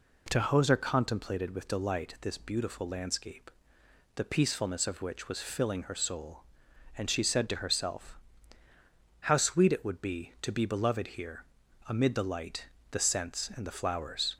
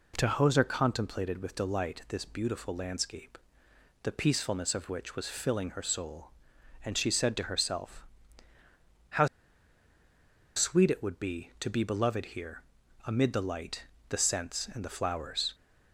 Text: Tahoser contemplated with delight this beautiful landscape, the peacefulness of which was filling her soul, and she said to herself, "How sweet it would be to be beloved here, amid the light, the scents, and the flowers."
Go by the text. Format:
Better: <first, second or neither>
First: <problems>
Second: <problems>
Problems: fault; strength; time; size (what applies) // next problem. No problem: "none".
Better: first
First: none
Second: pauses between "How" and "sweet"; strong; at 9.2 s; 1.2 s long